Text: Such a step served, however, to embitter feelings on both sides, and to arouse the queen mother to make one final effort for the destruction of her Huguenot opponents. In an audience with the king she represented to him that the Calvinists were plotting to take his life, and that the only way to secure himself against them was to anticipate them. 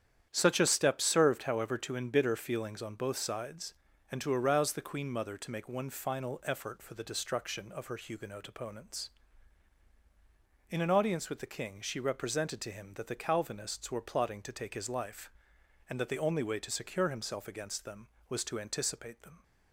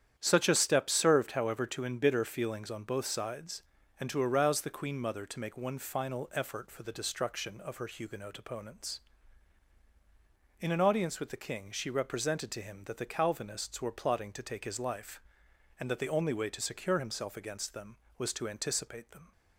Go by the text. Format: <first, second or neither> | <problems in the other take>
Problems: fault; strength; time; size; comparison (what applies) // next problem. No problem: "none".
neither | starts louder than the rest; strong; the same in both